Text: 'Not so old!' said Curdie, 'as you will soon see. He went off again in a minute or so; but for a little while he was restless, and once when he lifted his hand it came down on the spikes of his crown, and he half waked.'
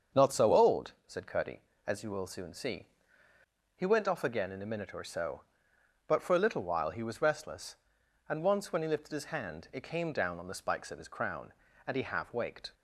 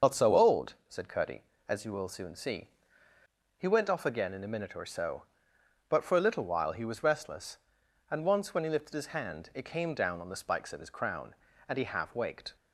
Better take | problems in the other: first | loses the start of "Not"; at 0.0 s; 65 ms // starts louder than the rest; until 1.1 s; 6.5 dB; also in the first

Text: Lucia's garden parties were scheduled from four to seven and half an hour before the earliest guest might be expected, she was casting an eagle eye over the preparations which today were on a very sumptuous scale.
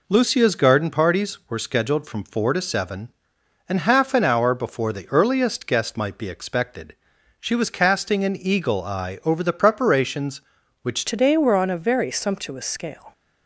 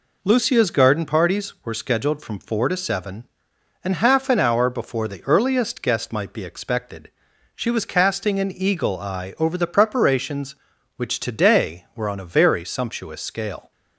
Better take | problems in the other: second | changes voice at "today"; from 11.0 s on; 2.1 s long

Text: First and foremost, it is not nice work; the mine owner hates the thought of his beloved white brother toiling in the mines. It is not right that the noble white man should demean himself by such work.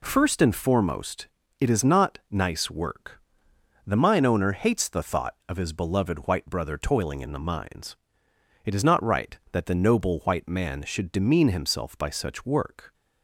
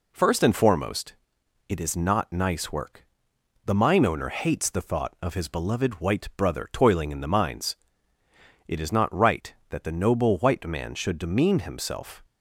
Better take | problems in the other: first | stops before "by such work"; at 12.2 s

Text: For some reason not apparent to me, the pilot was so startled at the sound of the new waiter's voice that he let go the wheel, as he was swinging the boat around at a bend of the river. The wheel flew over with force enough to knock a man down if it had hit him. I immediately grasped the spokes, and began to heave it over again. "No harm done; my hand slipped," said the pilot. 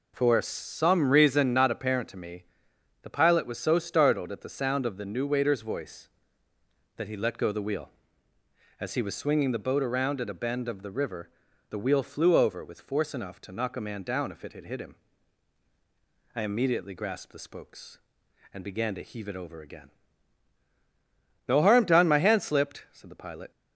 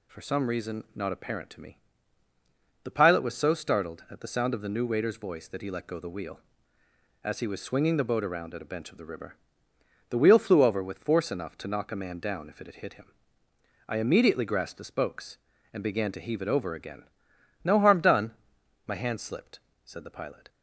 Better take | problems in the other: first | says "bench" for "bend"; at 8.7 s

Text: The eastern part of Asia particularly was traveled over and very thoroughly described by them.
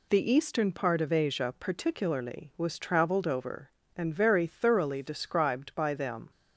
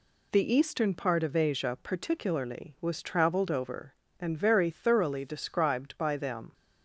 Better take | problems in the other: neither | none

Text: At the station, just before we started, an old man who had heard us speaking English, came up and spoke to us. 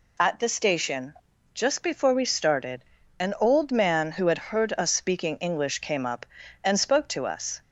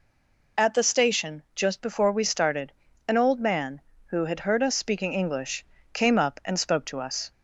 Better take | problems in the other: first | stays silent before the first word; slight; until 0.5 s; 0.5 s long

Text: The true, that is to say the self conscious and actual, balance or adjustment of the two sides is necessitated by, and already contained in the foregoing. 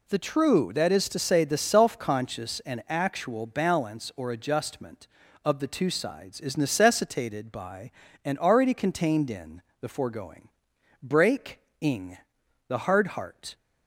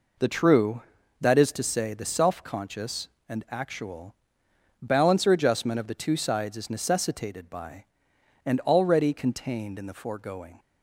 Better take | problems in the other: second | pauses between "in" and "the"; slight; at 9.6 s; 0.18 s long // goes on to say "Break ing the hard heart"; strong; from 11.0 s on; 2.5 s long

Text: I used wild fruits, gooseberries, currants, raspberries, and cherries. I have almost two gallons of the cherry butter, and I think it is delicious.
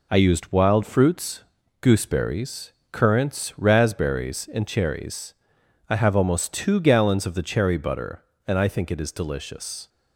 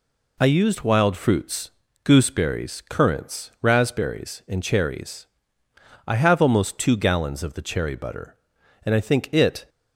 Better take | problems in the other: first | stops before "is delicious"; at 9.6 s

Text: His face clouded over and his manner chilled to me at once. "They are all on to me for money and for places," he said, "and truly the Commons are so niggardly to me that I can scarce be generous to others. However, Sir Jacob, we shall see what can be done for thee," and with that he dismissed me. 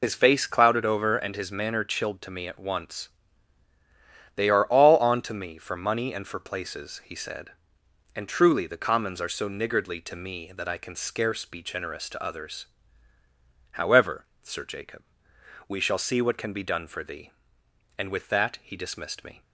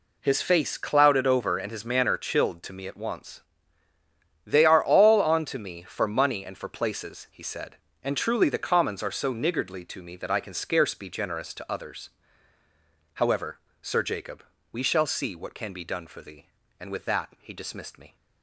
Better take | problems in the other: second | loses the start of "His"; at 0.0 s; 55 ms

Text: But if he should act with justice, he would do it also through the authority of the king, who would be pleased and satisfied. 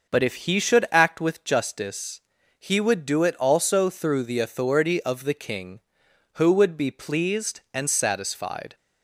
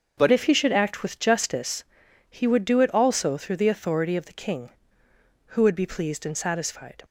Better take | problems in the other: first | changes voice at "if"; from 0.3 s on; 6.7 s long

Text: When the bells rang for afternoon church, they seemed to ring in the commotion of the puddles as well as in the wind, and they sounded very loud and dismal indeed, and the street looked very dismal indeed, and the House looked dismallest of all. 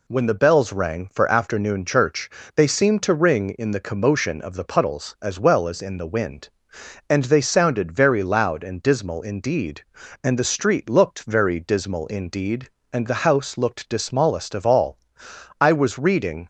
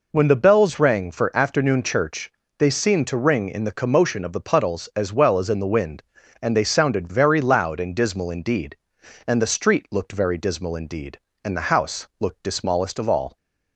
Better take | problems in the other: second | goes on to say "I was reading"; noticeable; from 15.5 s on; 0.88 s long

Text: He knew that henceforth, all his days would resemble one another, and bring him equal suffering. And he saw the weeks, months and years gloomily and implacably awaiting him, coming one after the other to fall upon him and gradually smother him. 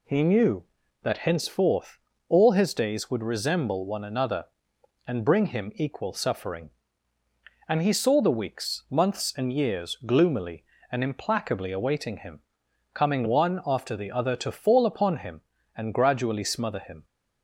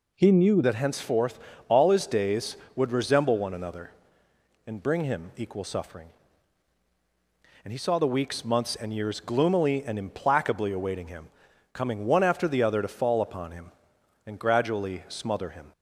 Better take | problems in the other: first | changes voice at "that"; from 0.6 s on; 15.1 s long

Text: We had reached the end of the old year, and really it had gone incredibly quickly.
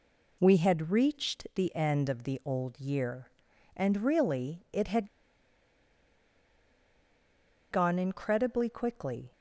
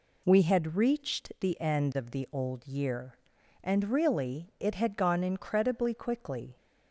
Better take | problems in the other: second | pauses between "had" and "gone"; strong; at 5.0 s; 2.6 s long

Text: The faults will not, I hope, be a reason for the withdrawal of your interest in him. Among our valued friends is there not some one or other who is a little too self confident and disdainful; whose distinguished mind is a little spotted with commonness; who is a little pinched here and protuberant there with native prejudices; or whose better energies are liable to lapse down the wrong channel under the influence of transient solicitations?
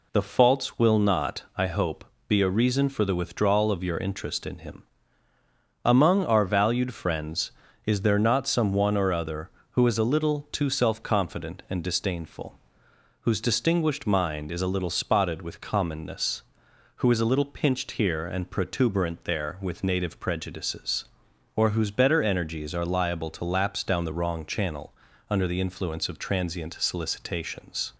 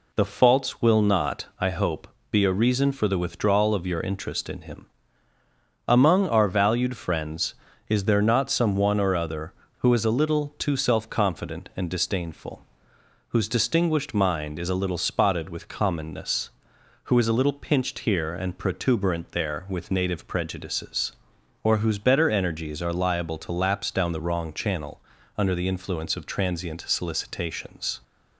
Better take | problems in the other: neither | pauses between "channel" and "under"; slight; the same in both

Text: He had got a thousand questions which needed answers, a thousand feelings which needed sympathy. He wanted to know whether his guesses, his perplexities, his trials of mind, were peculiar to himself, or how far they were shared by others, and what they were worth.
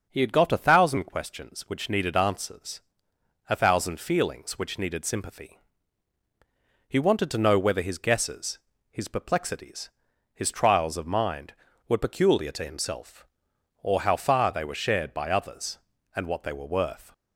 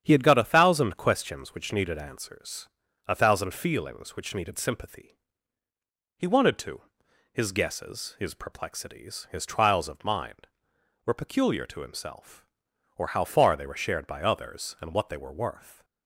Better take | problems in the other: first | starts louder than the rest; strong; until 1.0 s; 9 dB; also in the first // skips "know whether"; at 7.0 s

